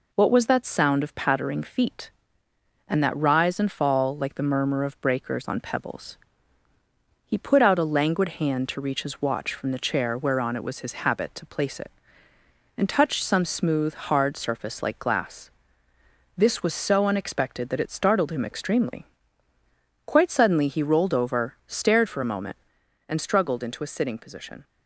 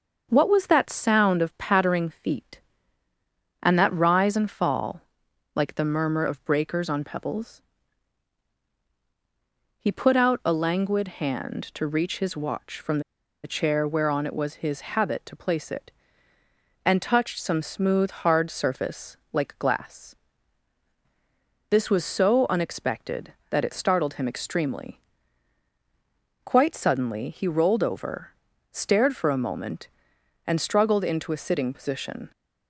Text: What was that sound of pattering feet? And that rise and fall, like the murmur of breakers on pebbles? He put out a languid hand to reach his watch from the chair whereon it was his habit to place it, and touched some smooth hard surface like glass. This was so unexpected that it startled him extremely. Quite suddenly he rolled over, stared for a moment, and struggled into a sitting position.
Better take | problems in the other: first | starts louder than the rest; until 1.3 s; 6.5 dB // pauses between "from" and "the"; at 12.9 s; 0.44 s long // pauses between "surface" and "like"; slight; at 19.1 s; 0.16 s long

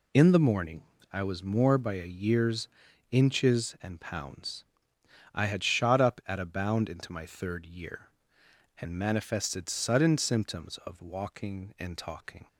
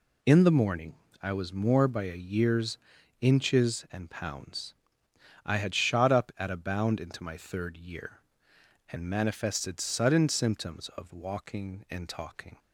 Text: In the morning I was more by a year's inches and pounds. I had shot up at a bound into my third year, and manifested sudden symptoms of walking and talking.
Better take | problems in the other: neither | pauses between "morning" and "I"; slight; the same in both // pauses between "year's" and "inches"; the same in both

